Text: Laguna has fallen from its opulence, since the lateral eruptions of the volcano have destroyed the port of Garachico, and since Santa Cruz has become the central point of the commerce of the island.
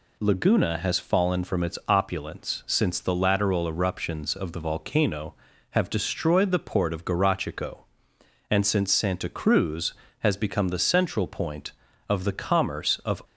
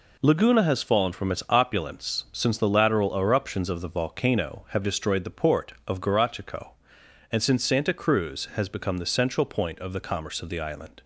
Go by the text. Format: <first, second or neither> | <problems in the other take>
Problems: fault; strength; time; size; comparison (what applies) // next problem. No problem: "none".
second | stops before "the island"; at 13.2 s